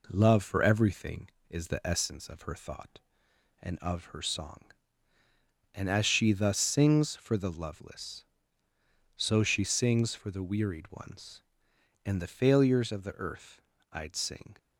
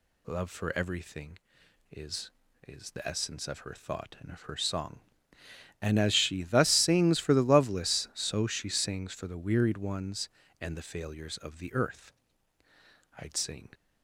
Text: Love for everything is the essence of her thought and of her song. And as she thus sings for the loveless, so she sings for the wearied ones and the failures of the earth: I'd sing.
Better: first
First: none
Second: says "is" twice; at 2.6 s

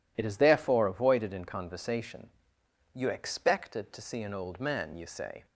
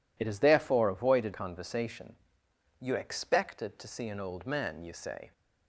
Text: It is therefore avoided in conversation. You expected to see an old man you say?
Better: first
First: none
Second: skips "in"; at 1.3 s

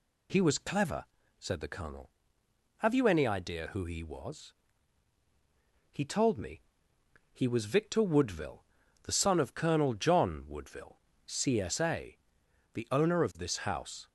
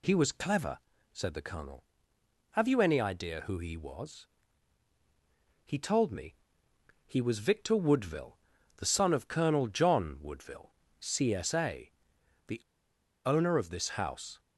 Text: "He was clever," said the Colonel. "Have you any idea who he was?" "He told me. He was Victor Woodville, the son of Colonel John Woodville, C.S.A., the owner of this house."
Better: first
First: none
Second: pauses between "the" and "owner"; noticeable; at 12.6 s; 0.66 s long

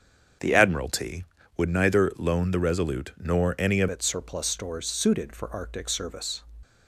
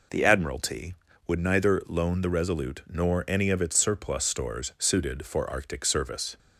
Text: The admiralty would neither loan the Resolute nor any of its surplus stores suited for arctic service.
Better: second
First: starts louder than the rest; strong; until 1.7 s; 7.5 dB // changes voice at "its"; from 3.9 s on; 2.5 s long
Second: none

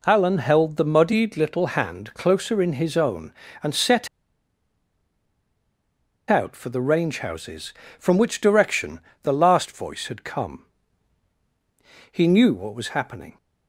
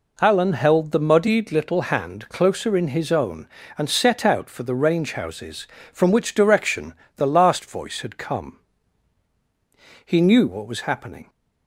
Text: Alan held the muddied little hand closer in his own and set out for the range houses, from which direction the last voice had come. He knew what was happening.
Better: second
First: pauses between "set" and "out"; strong; at 4.0 s; 2.2 s long // pauses between "direction" and "the"; slight; at 9.0 s; 0.22 s long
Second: pauses between "direction" and "the"; slight; at 6.9 s; 0.22 s long

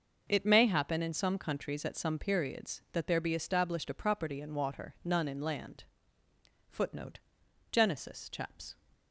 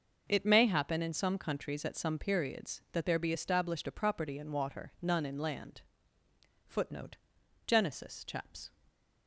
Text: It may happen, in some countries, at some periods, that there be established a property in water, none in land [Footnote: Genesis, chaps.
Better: neither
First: starts louder than the rest; noticeable; until 1.2 s; 6 dB // pauses between "land" and "Footnote"; noticeable; at 5.8 s; 0.84 s long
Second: starts louder than the rest; noticeable; until 1.2 s; 6 dB // pauses between "land" and "Footnote"; noticeable; at 5.8 s; 0.84 s long

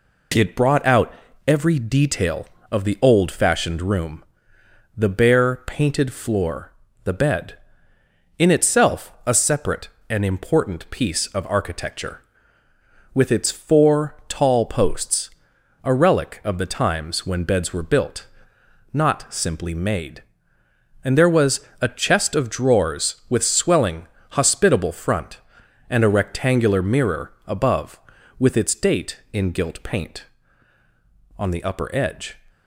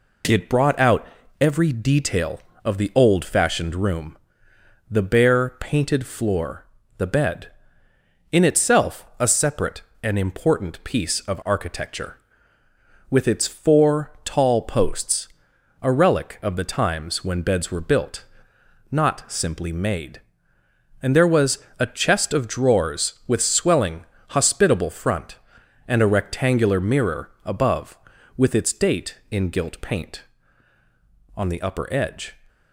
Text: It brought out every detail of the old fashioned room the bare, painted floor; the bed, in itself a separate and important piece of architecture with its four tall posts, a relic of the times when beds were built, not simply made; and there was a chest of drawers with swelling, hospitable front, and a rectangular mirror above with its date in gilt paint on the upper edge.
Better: neither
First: pauses between "out" and "every"; slight; at 1.1 s; 0.34 s long // pauses between "room" and "the"; noticeable; at 4.2 s; 0.70 s long // pauses between "was" and "a"; slight; at 21.5 s; 0.22 s long // pauses between "mirror" and "above"; slight; at 27.3 s; 0.16 s long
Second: pauses between "out" and "every"; slight; at 1.0 s; 0.34 s long // pauses between "room" and "the"; noticeable; at 4.1 s; 0.70 s long // pauses between "was" and "a"; slight; at 21.5 s; 0.22 s long // pauses between "mirror" and "above"; slight; at 27.3 s; 0.16 s long

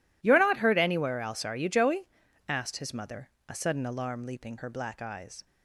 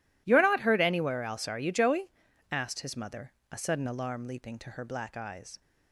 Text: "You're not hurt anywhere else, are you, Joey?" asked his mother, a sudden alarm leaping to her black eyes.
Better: second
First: skips "to"; at 4.5 s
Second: none

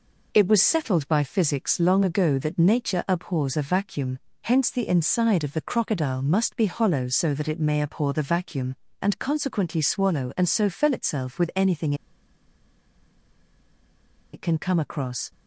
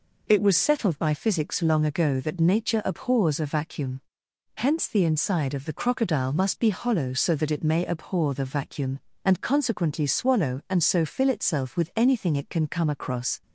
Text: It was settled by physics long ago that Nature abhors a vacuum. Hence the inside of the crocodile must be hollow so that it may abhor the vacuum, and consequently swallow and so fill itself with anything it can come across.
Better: second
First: pauses between "anything" and "it"; strong; at 11.9 s; 2.3 s long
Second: none

